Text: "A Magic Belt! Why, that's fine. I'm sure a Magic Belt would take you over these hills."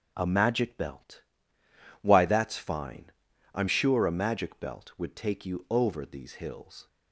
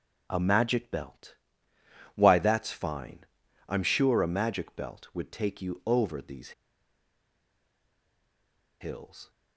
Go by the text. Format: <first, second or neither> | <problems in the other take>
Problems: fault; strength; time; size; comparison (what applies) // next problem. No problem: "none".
first | starts louder than the rest; until 1.2 s; 6.5 dB; also in the first // pauses between "these" and "hills"; strong; at 6.5 s; 2.2 s long